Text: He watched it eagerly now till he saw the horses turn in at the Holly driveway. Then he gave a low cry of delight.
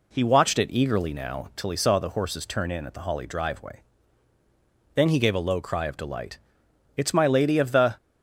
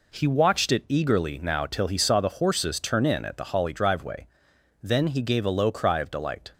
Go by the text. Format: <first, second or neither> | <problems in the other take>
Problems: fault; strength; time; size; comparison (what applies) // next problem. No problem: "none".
second | goes on to say "It's my Lady of the"; noticeable; from 6.9 s on; 0.98 s long